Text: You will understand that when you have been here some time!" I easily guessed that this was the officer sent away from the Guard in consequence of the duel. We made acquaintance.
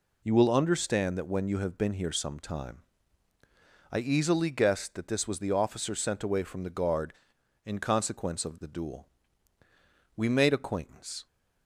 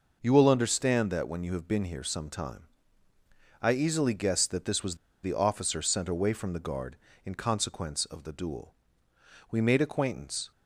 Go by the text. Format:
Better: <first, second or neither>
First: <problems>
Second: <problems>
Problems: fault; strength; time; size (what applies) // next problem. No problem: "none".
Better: first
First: none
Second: pauses between "was" and "the"; slight; at 4.9 s; 0.28 s long